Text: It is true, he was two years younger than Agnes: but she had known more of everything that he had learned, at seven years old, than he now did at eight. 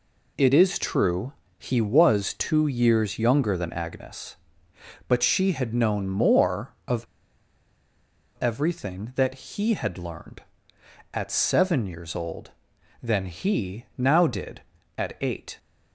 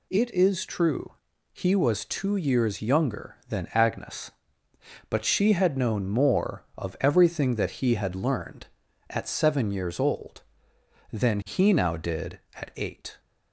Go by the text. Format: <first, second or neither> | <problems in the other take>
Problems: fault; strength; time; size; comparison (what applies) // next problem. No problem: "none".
second | pauses between "of" and "everything"; strong; at 7.0 s; 1.3 s long